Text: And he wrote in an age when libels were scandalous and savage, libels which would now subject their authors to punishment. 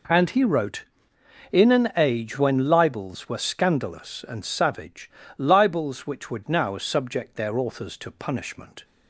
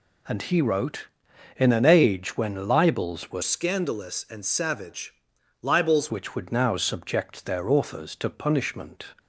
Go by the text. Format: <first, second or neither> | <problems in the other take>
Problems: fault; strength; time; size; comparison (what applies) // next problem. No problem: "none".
first | changes voice from "scandalous" to "libels"; from 3.4 to 6.1 s; 2.7 s long